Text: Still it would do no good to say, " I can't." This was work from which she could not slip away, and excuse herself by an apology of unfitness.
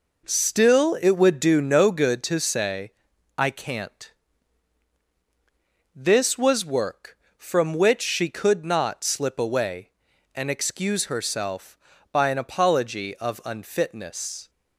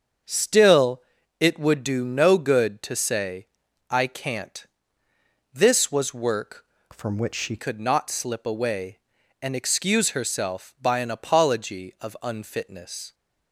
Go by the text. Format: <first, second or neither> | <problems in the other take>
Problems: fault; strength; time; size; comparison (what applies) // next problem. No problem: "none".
first | starts louder than the rest; until 1.6 s; 6.5 dB // pauses between "Still" and "it"; at 1.0 s; 0.38 s long // changes voice from "from" to "she"; from 6.9 to 7.5 s; 0.6 s long